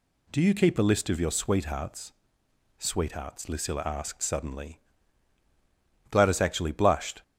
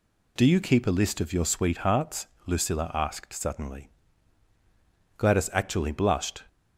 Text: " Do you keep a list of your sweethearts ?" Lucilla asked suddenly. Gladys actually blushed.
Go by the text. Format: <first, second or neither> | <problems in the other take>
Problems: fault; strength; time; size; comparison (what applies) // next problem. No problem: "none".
second | says "sweethearts" twice; at 2.7 s